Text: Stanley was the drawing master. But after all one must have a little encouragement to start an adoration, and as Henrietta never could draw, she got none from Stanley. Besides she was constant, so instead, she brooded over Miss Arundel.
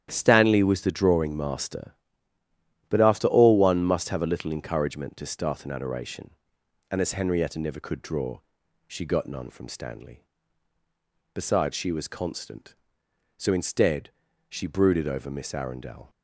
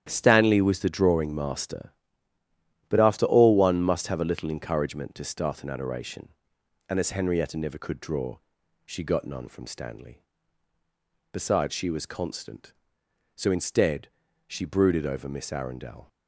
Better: neither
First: starts louder than the rest; strong; until 1.1 s; 10.5 dB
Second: starts louder than the rest; strong; until 1.1 s; 10.5 dB

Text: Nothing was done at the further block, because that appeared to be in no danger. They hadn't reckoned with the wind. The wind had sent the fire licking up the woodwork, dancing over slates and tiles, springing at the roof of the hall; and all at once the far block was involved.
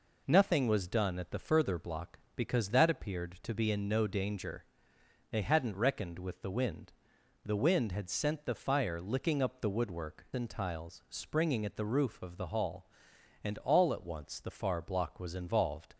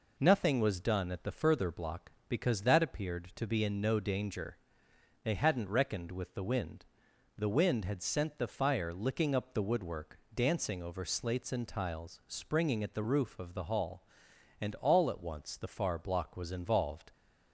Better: second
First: skips "dancing over slates"; at 10.2 s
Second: none

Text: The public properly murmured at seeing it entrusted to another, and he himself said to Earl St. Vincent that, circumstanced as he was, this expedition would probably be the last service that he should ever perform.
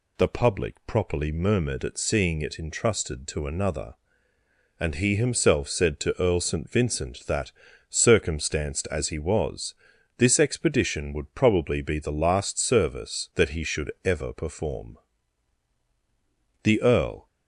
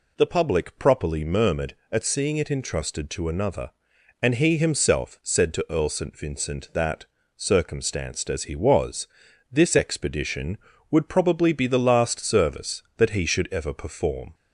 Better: second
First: goes on to say "The Earl"; noticeable; from 16.6 s on; 0.62 s long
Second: none

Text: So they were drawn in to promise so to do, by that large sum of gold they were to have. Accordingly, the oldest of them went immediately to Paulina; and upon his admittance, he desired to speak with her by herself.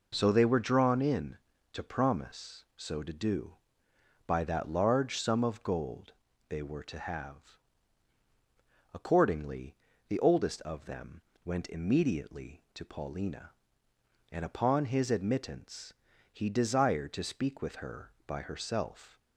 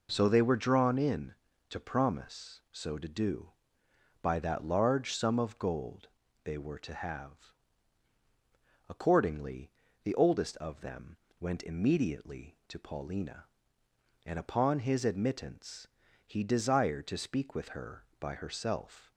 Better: neither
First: pauses between "gold" and "they"; slight; at 6.1 s; 0.34 s long // pauses between "them" and "went"; slight; at 11.2 s; 0.22 s long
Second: pauses between "gold" and "they"; slight; at 6.0 s; 0.34 s long // pauses between "them" and "went"; slight; at 11.1 s; 0.22 s long

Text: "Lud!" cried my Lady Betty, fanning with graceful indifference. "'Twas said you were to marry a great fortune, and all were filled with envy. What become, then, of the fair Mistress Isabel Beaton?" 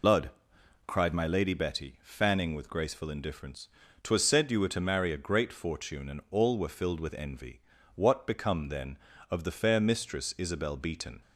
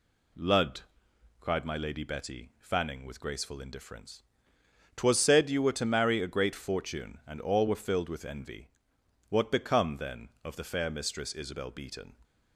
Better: second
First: loses the start of "Lud"; at 0.0 s; 100 ms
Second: none

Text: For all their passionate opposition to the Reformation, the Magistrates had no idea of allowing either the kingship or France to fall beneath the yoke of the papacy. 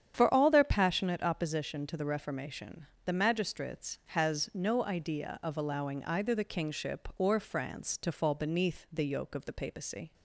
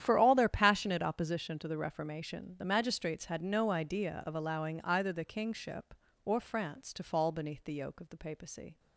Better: second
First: starts louder than the rest; strong; until 1.1 s; 8.5 dB // says "has" for "had"; at 4.0 s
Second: starts louder than the rest; strong; until 1.0 s; 10 dB

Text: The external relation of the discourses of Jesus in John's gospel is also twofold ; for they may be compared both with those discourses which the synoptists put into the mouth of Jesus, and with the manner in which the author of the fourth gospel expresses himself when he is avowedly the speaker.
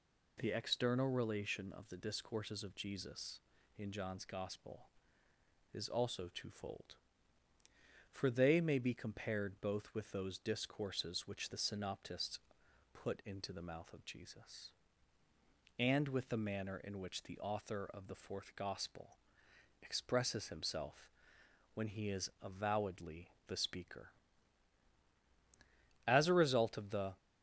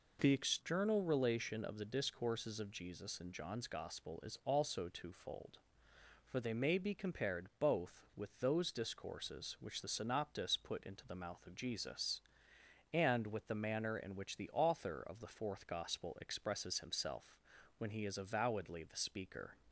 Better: second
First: pauses between "synoptists" and "put"; noticeable; at 12.3 s; 0.54 s long // pauses between "gospel" and "expresses"; noticeable; at 19.1 s; 0.64 s long // pauses between "himself" and "when"; noticeable; at 21.0 s; 0.64 s long // pauses between "avowedly" and "the"; slight; at 23.2 s; 0.18 s long // goes on to say "As a result of the"; noticeable; from 26.0 s on; 1.1 s long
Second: pauses between "himself" and "when"; at 17.3 s; 0.42 s long

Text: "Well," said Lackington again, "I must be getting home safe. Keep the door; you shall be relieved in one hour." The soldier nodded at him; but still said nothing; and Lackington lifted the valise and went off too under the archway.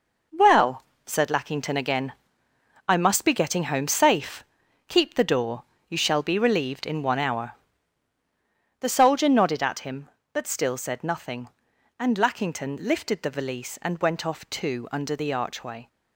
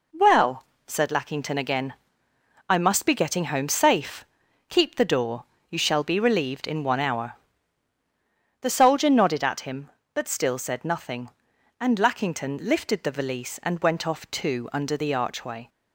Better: second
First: gets quieter; strong; throughout; 8 dB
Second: none

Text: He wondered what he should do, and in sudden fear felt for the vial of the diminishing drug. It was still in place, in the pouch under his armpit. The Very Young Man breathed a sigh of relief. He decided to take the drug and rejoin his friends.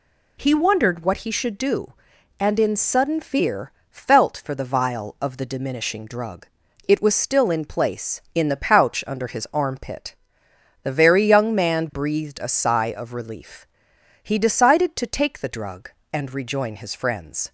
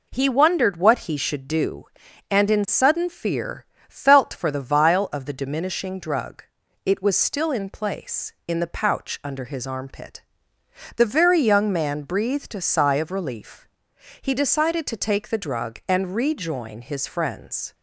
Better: neither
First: pauses between "fear" and "felt"; slight; at 3.7 s; 0.18 s long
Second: pauses between "fear" and "felt"; slight; at 3.6 s; 0.22 s long

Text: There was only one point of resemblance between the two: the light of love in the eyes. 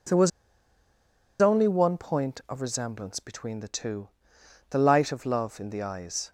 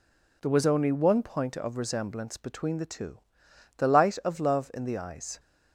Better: second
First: pauses between "was" and "only"; at 0.3 s; 1.1 s long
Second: none

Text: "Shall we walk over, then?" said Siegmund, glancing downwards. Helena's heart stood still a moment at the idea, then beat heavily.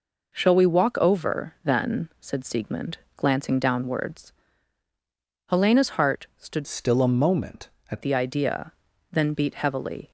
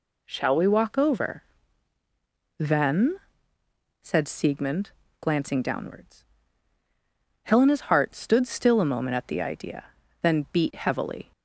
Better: second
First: changes voice from "still" to "at"; from 6.6 to 8.0 s; 1.4 s long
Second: none

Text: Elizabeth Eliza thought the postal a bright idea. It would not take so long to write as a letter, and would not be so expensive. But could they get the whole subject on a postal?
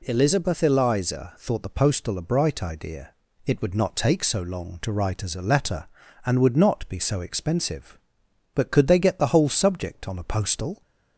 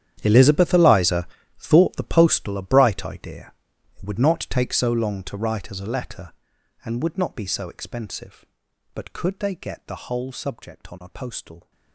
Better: first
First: none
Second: gets quieter; strong; throughout; 18 dB // pauses between "Eliza" and "thought"; slight; at 1.2 s; 0.32 s long

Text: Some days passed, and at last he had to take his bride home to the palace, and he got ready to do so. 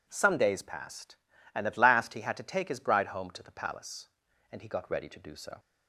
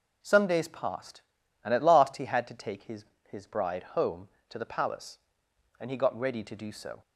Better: first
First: none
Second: says "his" twice; at 3.2 s

